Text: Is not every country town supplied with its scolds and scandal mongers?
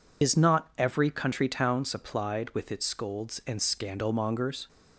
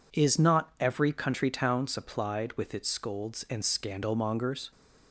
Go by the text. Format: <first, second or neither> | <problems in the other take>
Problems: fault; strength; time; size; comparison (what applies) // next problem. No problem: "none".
second | loses the start of "Is"; at 0.2 s; 110 ms